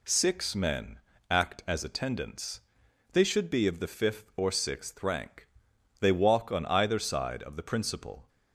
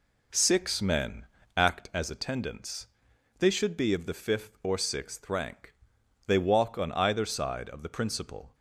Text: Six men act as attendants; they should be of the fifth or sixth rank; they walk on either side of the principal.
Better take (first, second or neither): first